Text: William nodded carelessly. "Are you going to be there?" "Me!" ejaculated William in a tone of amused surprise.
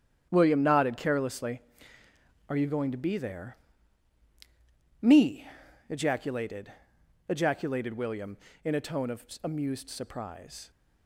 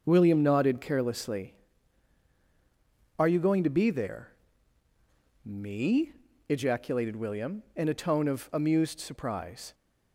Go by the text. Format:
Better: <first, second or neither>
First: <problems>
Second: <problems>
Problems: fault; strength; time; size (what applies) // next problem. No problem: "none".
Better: second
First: starts louder than the rest; strong; until 1.3 s; 8.5 dB // says "ejaculated" twice; at 7.3 s // pauses between "of" and "amused"; slight; at 9.2 s; 0.18 s long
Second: starts louder than the rest; noticeable; until 1.0 s; 6 dB